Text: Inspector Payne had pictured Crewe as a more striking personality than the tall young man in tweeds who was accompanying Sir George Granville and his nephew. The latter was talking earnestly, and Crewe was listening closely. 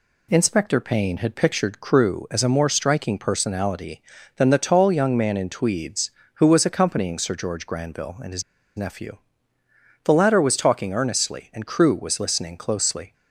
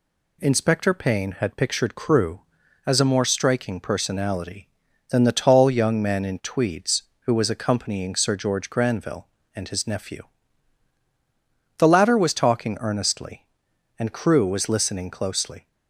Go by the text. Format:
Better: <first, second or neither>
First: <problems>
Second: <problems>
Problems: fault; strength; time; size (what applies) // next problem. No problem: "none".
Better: second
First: pauses between "his" and "nephew"; slight; at 8.4 s; 0.34 s long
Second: none